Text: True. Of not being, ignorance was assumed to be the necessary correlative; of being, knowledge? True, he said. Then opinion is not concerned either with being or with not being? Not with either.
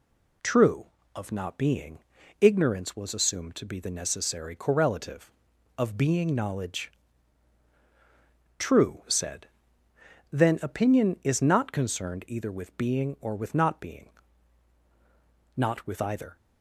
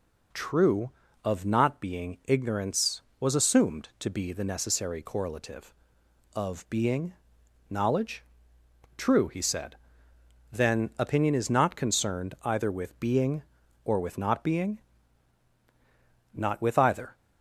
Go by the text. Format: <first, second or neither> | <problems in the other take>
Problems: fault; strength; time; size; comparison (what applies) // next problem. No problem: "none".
second | skips "he"; at 9.0 s